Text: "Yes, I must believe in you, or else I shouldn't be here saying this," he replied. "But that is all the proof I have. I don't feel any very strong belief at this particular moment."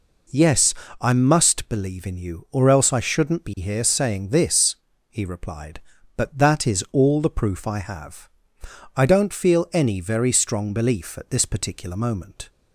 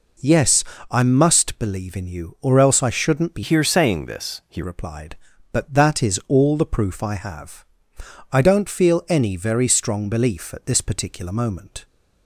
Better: first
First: none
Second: changes voice from "here" to "he"; from 3.4 to 4.6 s; 1.2 s long

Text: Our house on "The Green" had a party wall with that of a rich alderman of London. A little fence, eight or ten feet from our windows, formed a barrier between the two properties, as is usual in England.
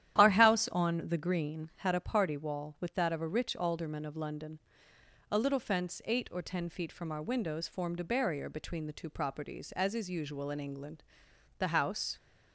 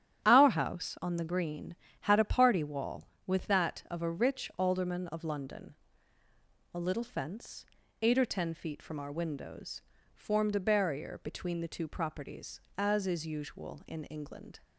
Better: second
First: starts louder than the rest; strong; until 1.2 s; 11.5 dB // goes on to say "The house"; from 11.5 s on; 0.58 s long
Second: starts louder than the rest; strong; until 1.2 s; 10 dB

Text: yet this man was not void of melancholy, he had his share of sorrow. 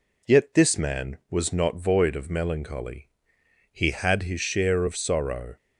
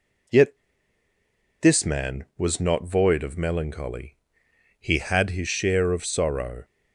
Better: first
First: none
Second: pauses between "yet" and "this"; at 0.5 s; 1.0 s long

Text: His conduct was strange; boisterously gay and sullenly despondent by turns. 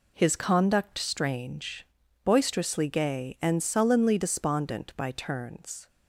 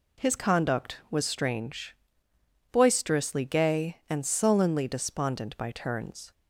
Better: second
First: skips "was"; at 0.9 s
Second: none

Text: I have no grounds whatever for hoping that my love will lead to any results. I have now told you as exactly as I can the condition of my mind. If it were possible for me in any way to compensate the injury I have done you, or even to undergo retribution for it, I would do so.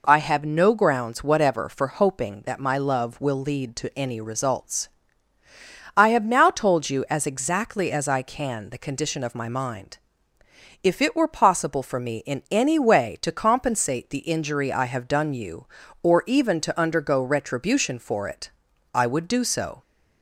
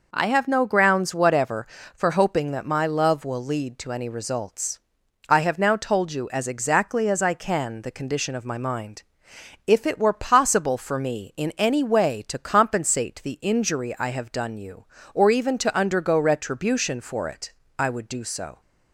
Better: neither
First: none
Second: none

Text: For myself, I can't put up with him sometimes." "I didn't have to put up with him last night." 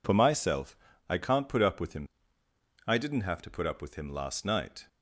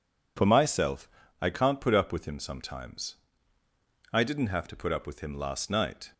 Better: second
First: skips "sometimes"; at 2.4 s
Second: none

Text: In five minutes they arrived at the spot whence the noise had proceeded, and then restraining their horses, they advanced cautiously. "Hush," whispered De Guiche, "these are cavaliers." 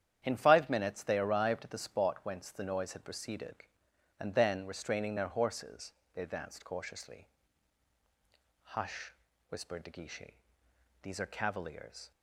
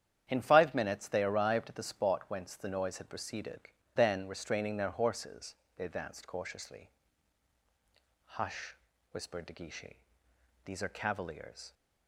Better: first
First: starts louder than the rest; strong; until 1.2 s; 9.5 dB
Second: starts louder than the rest; strong; until 1.2 s; 9.5 dB // skips "and"; at 3.7 s

